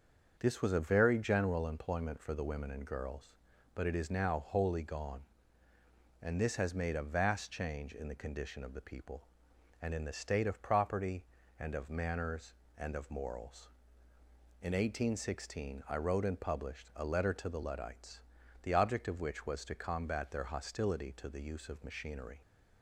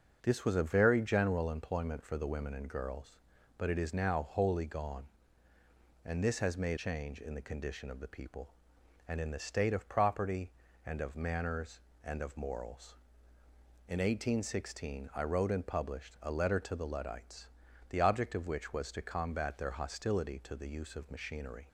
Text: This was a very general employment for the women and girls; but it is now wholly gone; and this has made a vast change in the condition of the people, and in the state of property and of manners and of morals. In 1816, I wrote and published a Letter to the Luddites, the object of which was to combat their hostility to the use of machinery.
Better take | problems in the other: first | starts louder than the rest; until 1.2 s; 6 dB; also in the first // skips "a vast"; at 6.7 s

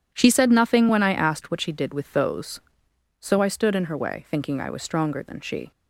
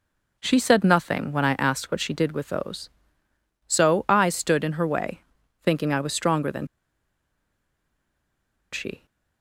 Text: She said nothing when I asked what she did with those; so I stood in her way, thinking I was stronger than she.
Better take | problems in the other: first | pauses between "than" and "she"; strong; at 6.6 s; 2.0 s long

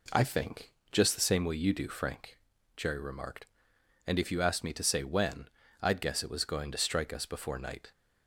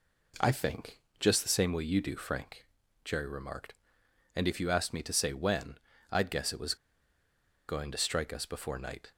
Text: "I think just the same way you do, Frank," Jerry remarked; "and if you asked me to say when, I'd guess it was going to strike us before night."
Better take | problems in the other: first | pauses between "think" and "just"; slight; at 0.9 s; 0.20 s long; slight in the first // pauses between "was" and "going"; noticeable; at 6.7 s; 0.93 s long

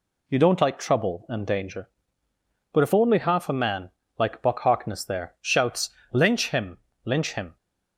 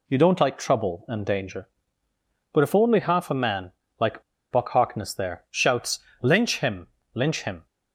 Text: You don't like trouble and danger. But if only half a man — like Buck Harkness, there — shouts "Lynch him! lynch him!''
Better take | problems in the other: first | pauses between "like" and "Buck"; slight; at 4.2 s; 0.29 s long // pauses between "shouts" and "Lynch"; slight; at 5.9 s; 0.22 s long; slight in the first

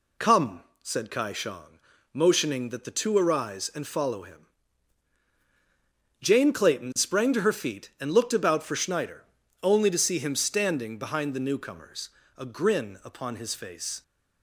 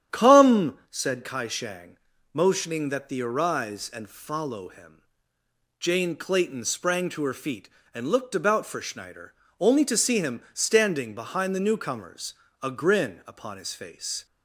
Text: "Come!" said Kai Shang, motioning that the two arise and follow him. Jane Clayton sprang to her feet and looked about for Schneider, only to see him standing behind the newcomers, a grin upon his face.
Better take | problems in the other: first | starts louder than the rest; strong; until 1.2 s; 9.5 dB // skips "two"; at 3.2 s

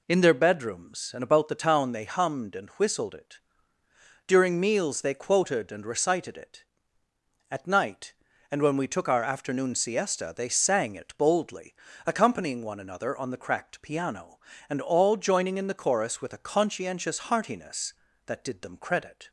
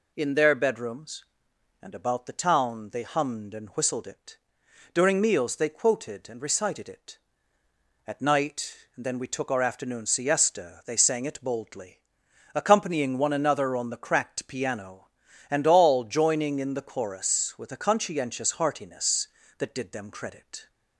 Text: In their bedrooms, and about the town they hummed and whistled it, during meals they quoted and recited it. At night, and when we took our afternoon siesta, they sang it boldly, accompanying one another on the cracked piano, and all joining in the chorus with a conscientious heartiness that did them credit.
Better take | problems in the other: first | says "then" for "when"; at 9.0 s

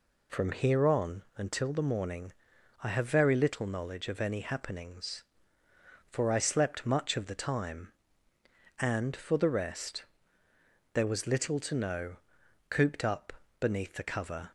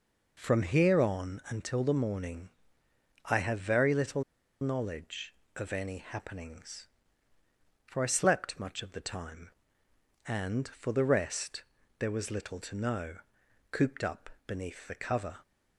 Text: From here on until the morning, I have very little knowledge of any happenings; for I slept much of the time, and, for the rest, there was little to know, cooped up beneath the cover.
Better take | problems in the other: first | pauses between "little" and "knowledge"; at 4.2 s; 0.39 s long // pauses between "up" and "beneath"; slight; at 14.2 s; 0.18 s long; slight in the first

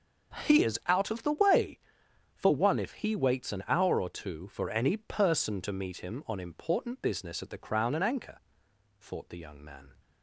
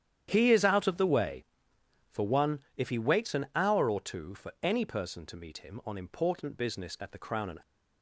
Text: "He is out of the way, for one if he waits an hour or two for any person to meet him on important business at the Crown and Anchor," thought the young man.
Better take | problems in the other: first | starts louder than the rest; strong; until 1.3 s; 10 dB; strong in the first // pauses between "one" and "if"; slight; at 2.5 s; 0.18 s long // stops before "Anchor thought the young man"; at 7.6 s

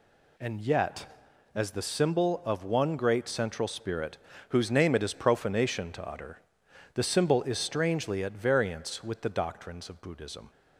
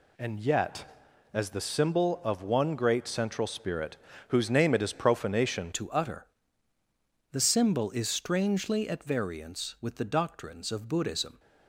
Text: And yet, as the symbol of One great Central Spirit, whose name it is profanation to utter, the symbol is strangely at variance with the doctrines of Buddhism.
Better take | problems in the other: first | changes voice at "to"; from 5.7 s on; 5.6 s long

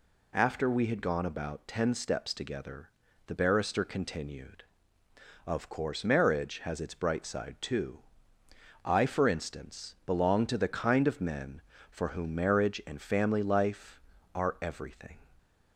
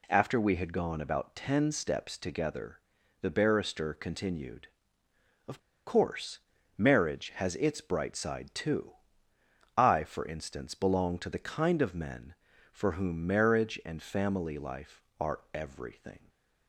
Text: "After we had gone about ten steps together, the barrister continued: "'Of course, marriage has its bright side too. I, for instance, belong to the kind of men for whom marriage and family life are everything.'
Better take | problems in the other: first | pauses between "Of" and "course"; slight; at 5.5 s; 0.28 s long

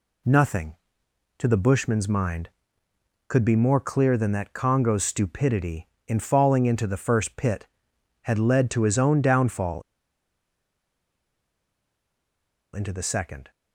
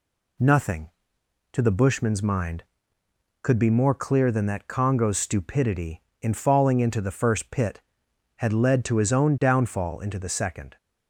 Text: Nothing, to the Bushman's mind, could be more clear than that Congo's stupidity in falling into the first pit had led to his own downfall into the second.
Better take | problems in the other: second | pauses between "downfall" and "into"; strong; at 9.8 s; 2.9 s long

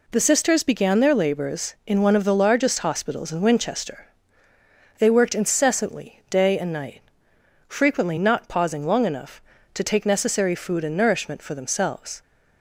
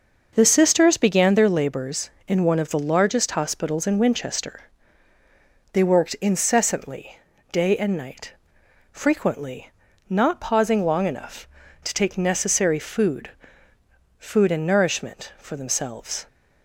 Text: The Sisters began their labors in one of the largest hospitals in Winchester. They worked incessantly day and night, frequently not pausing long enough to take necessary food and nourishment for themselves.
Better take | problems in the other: first | starts louder than the rest; noticeable; until 1.3 s; 6 dB // pauses between "incessantly" and "day"; slight; at 7.1 s; 0.32 s long // pauses between "frequently" and "not"; at 9.7 s; 0.38 s long // says "food" twice; at 14.1 s

